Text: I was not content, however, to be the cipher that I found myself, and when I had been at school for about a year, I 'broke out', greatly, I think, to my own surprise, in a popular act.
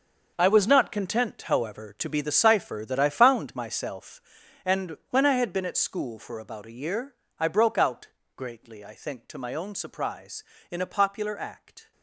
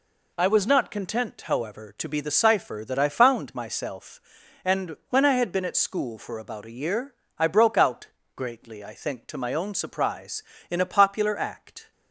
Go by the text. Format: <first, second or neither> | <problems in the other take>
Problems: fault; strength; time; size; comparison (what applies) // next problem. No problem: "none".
second | gets quieter; strong; throughout; 12.5 dB